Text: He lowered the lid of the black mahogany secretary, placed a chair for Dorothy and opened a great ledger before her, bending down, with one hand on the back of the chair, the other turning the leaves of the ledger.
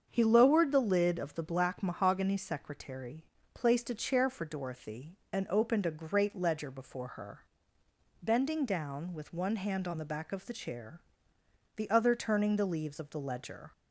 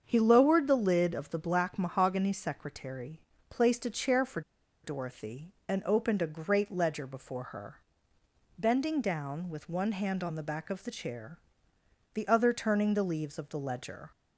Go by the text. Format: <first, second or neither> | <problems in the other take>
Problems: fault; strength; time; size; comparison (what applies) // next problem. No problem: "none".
first | starts louder than the rest; strong; until 1.0 s; 7.5 dB; strong in the first // pauses between "for" and "Dorothy"; at 4.4 s; 0.43 s long